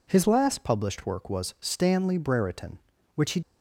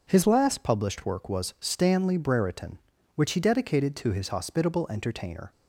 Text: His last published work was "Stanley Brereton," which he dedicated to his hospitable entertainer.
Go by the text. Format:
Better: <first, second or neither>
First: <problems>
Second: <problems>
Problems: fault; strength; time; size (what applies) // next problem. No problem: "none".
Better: second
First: stops before "dedicated to his hospitable entertainer"; at 3.4 s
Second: none